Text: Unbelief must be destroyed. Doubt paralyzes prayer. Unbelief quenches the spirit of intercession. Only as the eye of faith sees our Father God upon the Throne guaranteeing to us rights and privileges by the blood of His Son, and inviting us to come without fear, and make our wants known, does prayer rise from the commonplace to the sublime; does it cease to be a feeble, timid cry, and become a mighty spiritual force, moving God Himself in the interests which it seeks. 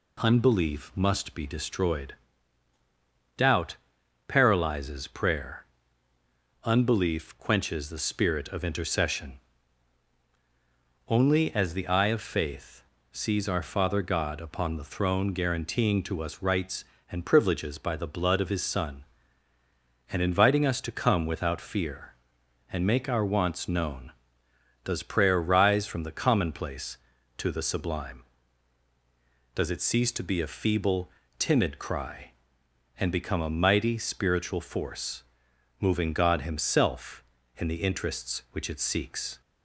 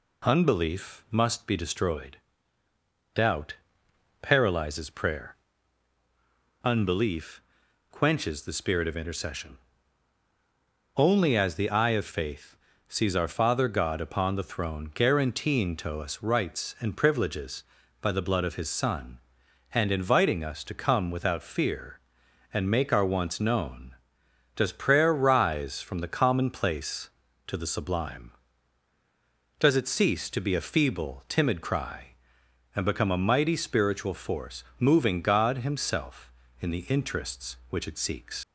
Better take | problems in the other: first | pauses between "Doubt" and "paralyzes"; noticeable; at 3.5 s; 0.66 s long; noticeable in the first // pauses between "Unbelief" and "quenches"; noticeable; at 7.4 s; 0.50 s long // pauses between "faith" and "sees"; slight; at 12.5 s; 0.32 s long; slight in the first // leaves "seeks" unfinished; at 38.4 s; 140 ms

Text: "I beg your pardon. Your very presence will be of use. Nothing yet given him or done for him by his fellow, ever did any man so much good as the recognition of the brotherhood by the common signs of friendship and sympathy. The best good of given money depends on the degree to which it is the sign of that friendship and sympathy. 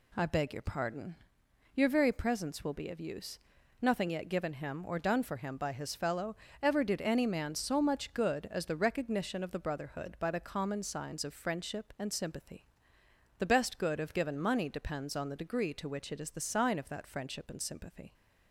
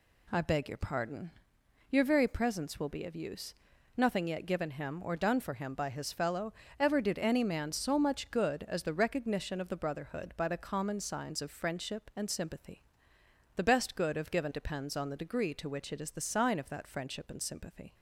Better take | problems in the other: first | skips "money"; at 14.5 s

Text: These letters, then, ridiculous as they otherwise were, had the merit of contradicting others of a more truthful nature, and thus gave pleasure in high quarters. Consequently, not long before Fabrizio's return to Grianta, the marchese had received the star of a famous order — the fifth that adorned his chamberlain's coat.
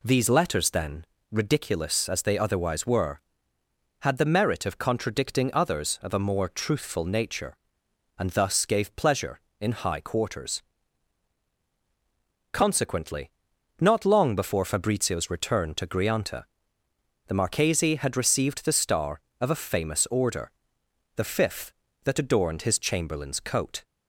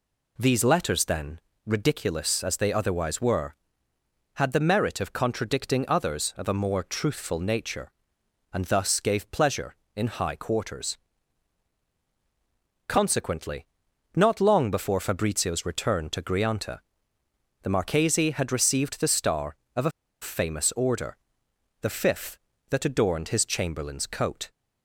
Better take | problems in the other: first | pauses between "a" and "famous"; slight; at 19.9 s; 0.30 s long

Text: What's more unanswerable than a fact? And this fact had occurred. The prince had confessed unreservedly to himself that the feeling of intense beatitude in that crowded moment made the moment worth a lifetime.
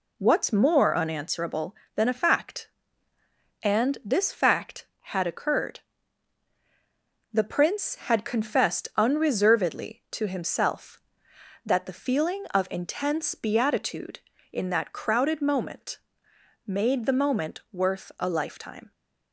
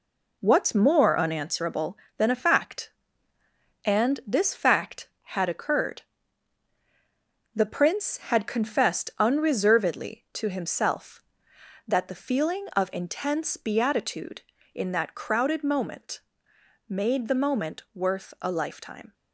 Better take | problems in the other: first | gets quieter; throughout; 6 dB // pauses between "moment" and "made"; noticeable; at 16.2 s; 0.66 s long; noticeable in the first

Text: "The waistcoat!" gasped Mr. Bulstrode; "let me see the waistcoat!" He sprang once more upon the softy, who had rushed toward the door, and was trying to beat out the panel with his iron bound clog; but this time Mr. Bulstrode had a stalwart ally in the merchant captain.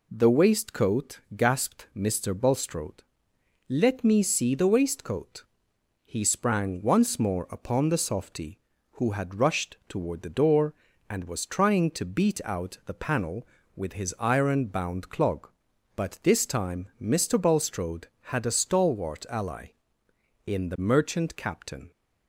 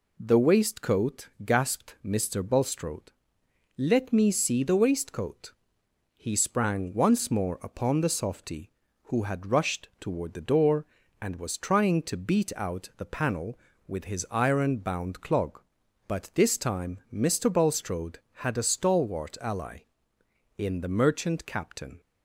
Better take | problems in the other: neither | none

